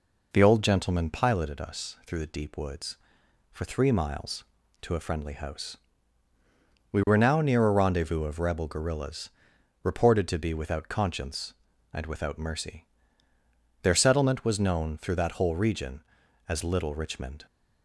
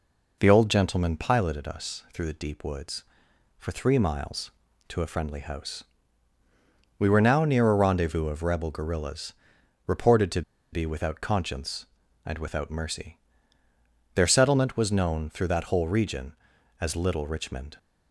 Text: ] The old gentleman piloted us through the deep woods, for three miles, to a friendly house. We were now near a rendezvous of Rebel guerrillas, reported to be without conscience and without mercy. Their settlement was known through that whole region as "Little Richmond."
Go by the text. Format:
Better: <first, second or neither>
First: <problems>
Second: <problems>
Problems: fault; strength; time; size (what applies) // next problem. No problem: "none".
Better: first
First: none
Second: pauses between "to" and "be"; slight; at 10.4 s; 0.31 s long